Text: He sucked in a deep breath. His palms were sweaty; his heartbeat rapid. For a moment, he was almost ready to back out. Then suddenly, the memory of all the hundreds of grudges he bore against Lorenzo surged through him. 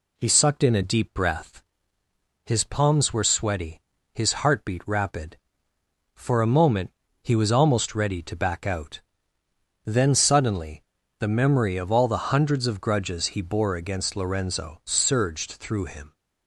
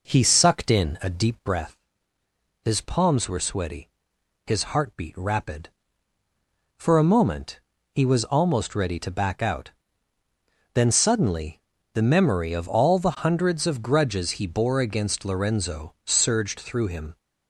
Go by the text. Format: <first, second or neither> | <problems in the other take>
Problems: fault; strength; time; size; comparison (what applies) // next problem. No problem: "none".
first | starts louder than the rest; noticeable; until 1.6 s; 4.5 dB